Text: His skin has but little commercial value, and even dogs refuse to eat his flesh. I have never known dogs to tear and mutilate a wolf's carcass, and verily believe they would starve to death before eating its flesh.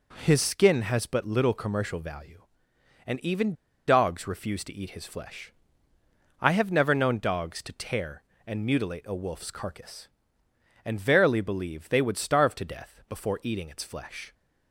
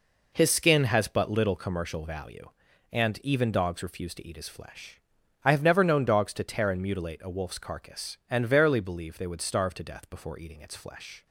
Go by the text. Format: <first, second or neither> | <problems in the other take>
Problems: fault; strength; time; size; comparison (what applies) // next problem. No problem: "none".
second | pauses between "even" and "dogs"; slight; at 3.5 s; 0.34 s long